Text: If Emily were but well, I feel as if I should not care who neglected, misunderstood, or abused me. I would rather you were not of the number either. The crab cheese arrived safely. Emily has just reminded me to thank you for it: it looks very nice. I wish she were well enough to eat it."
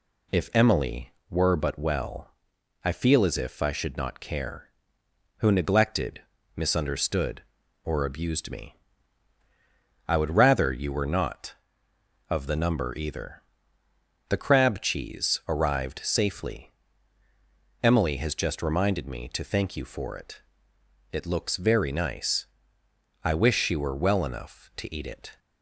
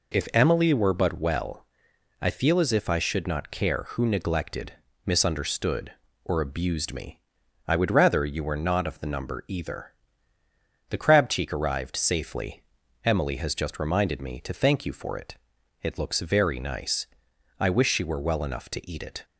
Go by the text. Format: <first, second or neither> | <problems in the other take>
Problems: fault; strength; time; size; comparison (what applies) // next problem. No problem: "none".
first | says "cheek" for "cheese"; at 11.3 s